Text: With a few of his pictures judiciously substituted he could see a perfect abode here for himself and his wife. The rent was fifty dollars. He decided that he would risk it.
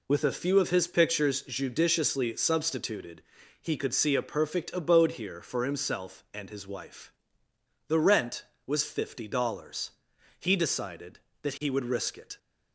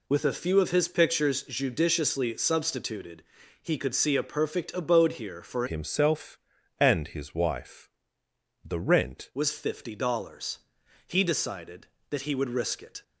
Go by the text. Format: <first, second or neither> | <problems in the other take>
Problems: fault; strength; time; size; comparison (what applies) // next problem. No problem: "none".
first | pauses between "substituted" and "he"; slight; at 3.2 s; 0.36 s long; slight in the first // changes voice from "himself" to "rent"; from 5.6 to 9.3 s; 3.7 s long